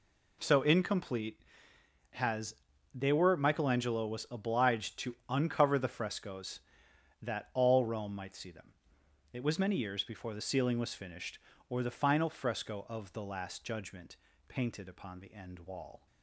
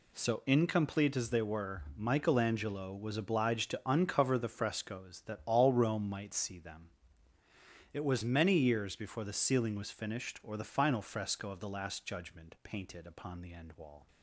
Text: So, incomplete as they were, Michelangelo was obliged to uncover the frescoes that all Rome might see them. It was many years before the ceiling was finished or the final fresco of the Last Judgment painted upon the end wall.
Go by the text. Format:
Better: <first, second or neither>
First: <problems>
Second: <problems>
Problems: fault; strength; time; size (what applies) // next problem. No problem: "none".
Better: second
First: says "has" for "as"; at 2.1 s // pauses between "Judgment" and "painted"; slight; at 14.1 s; 0.32 s long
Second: none